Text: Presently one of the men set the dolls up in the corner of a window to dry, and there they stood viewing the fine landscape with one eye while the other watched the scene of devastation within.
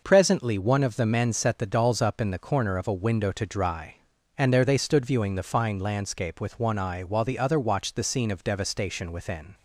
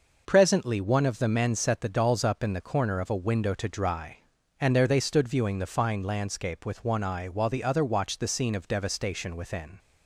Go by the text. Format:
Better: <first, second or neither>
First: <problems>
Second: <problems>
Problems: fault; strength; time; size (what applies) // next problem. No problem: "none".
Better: neither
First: none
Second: none